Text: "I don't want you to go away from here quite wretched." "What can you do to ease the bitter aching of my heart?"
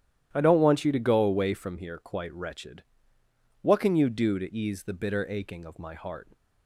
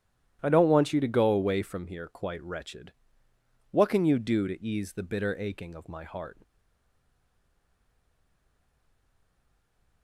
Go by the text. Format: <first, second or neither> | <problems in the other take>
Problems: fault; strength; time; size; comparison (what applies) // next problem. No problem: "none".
first | starts louder than the rest; strong; until 1.4 s; 11.5 dB; strong in the first // stays silent after the last word; strong; from 6.4 s on; 3.6 s long